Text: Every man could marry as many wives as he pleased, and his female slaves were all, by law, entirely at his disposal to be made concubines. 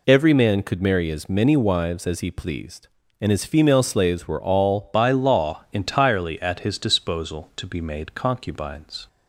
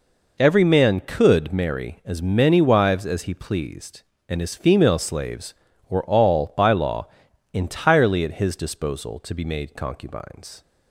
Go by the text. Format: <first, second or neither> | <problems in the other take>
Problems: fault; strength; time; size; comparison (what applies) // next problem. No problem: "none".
second | changes voice at "by"; from 4.9 s on; 4.1 s long